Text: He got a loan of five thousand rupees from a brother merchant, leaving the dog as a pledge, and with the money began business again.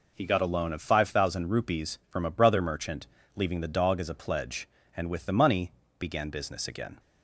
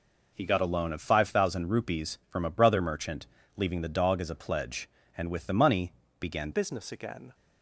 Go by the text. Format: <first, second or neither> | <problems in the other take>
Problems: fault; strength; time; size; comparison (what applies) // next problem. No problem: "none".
first | pauses between "money" and "began"; slight; at 5.9 s; 0.26 s long; slight in the first // changes voice at "business"; from 6.5 s on; 0.8 s long